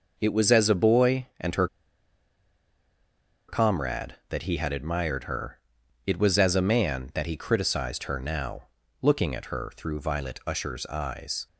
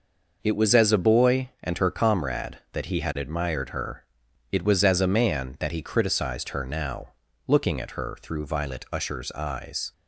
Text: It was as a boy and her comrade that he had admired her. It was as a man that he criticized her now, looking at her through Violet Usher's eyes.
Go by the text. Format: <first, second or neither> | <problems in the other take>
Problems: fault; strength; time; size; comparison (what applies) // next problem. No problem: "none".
second | pauses between "her" and "comrade"; strong; at 1.6 s; 1.8 s long